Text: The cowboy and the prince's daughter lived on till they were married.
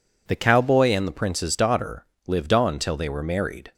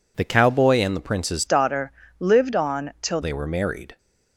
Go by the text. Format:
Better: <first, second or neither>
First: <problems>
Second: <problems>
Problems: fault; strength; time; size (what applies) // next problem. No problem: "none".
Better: first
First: pauses between "daughter" and "lived"; slight; at 2.0 s; 0.20 s long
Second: changes voice from "daughter" to "till"; from 1.4 to 3.2 s; 1.8 s long // pauses between "daughter" and "lived"; slight; at 1.9 s; 0.30 s long